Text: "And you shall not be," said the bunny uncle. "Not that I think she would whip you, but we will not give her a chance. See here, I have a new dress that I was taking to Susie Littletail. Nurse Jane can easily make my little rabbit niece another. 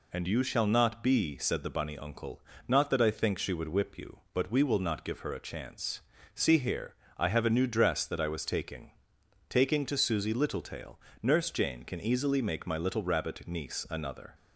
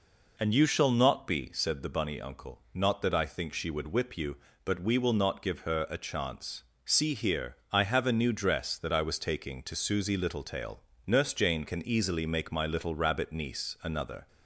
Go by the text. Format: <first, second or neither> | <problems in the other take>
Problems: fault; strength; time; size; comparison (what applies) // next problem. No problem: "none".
second | says "taking" twice; at 9.4 s